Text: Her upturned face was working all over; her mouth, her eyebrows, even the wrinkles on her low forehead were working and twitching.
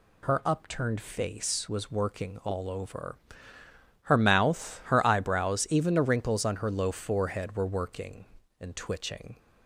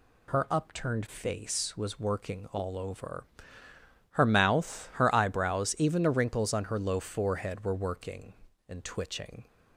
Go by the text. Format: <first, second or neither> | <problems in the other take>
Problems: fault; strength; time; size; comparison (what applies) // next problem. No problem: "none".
neither | none